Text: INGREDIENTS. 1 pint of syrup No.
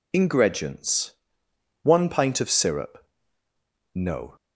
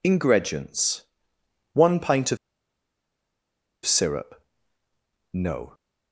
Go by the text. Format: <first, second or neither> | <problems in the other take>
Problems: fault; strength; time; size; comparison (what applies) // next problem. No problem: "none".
first | pauses between "of" and "syrup"; strong; at 2.3 s; 1.4 s long // pauses between "syrup" and "No"; noticeable; at 4.3 s; 0.94 s long; noticeable in the first